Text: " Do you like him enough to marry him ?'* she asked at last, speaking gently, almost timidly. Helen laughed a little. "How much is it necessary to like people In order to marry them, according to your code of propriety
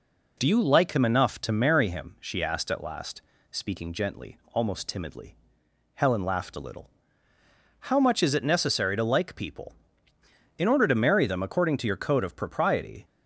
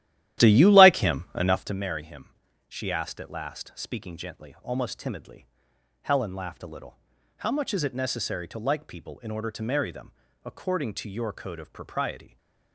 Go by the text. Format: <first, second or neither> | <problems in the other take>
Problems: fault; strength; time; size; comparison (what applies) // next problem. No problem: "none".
first | starts louder than the rest; strong; until 1.8 s; 13 dB